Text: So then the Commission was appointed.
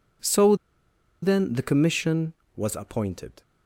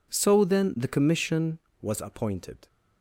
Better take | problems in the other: second | pauses between "So" and "then"; noticeable; at 0.5 s; 0.67 s long

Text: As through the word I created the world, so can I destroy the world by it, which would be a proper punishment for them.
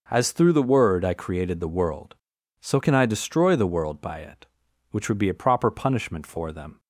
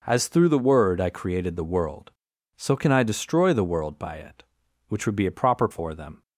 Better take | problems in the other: first | skips "punishment"; at 5.6 s

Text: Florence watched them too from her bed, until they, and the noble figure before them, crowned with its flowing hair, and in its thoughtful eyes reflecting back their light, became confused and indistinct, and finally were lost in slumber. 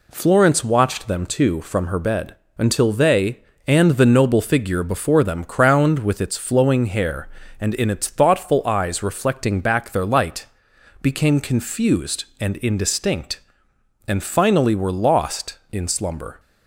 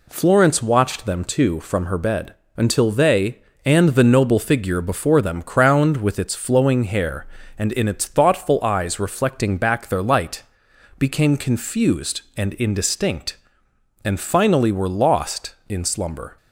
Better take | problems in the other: neither | none

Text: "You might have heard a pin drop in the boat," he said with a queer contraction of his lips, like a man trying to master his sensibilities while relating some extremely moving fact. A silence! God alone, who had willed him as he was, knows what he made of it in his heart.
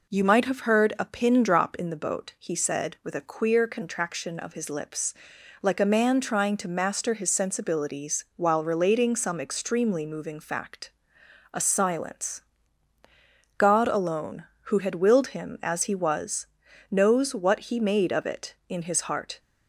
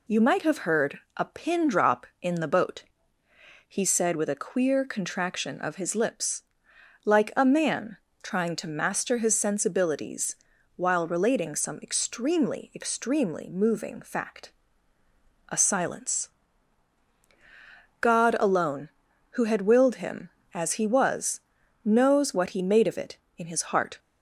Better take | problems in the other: first | pauses between "heard" and "a"; slight; at 1.0 s; 0.16 s long // pauses between "man" and "trying"; slight; at 7.9 s; 0.26 s long // pauses between "sensibilities" and "while"; at 10.3 s; 0.40 s long // says "extremely" twice; at 12.7 s

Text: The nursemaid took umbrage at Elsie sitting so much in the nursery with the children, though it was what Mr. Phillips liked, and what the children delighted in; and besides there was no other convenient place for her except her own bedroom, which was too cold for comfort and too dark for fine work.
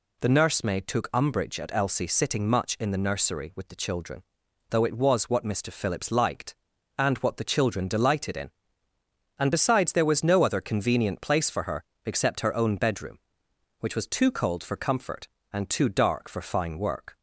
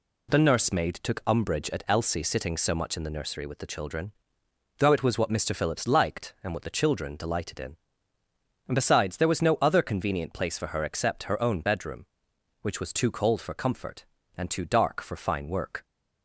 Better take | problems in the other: second | skips "so"; at 2.4 s // pauses between "her" and "except"; slight; at 11.8 s; 0.22 s long

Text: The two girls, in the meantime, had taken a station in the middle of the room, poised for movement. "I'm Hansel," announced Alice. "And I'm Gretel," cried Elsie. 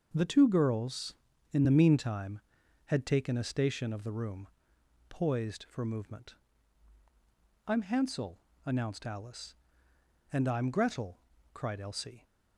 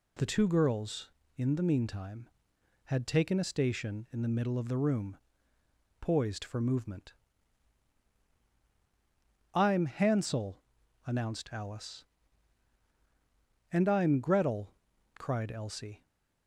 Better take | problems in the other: second | starts louder than the rest; noticeable; until 1.1 s; 6 dB // skips "in the middle"; at 3.9 s

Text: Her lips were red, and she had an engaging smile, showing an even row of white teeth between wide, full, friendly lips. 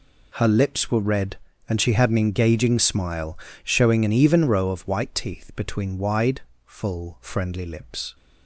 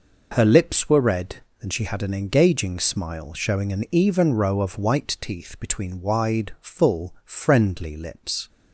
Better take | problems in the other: neither | none

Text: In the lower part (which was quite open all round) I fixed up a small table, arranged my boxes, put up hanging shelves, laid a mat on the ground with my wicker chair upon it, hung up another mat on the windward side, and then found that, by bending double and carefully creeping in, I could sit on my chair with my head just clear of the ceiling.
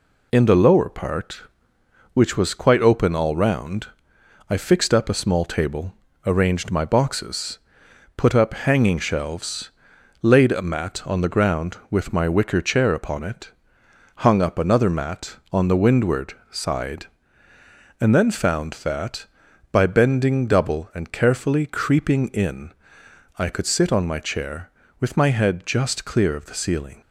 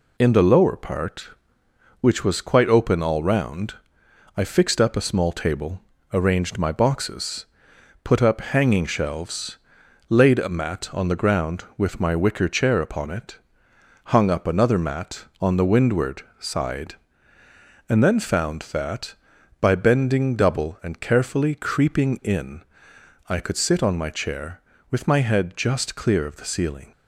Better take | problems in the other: neither | pauses between "windward" and "side"; slight; the same in both

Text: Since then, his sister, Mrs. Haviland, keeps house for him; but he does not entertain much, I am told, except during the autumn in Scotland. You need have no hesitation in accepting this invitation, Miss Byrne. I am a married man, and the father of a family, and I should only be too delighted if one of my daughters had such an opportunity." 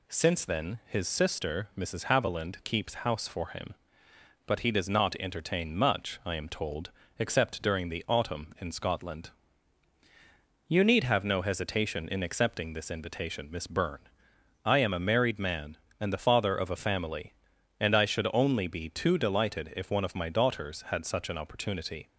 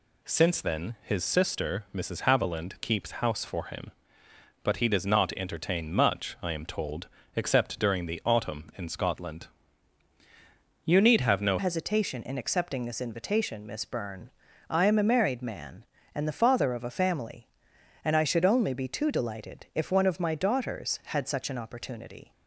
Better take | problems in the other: first | changes voice at "hesitation"; from 11.5 s on; 10.8 s long

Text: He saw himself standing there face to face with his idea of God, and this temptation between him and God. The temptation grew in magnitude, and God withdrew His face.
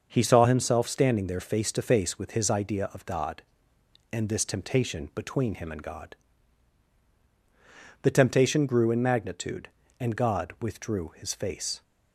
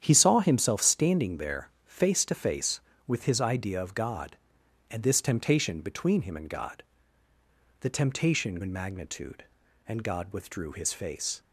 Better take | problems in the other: first | starts louder than the rest; strong; until 1.0 s; 9 dB; also in the first // skips "grew"; at 8.6 s

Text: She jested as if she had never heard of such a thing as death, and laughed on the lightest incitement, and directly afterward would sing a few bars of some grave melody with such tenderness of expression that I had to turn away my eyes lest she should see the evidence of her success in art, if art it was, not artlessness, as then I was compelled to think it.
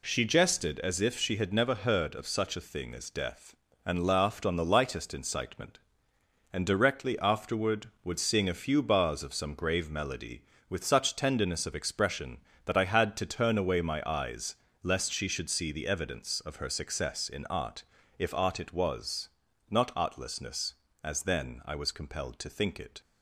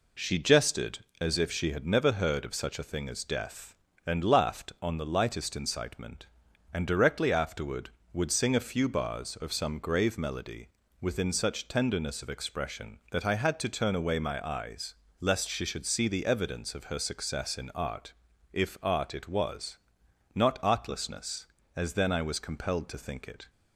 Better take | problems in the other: first | says "within" for "with"; at 10.9 s // pauses between "eyes" and "lest"; slight; at 14.9 s; 0.24 s long; slight in the first

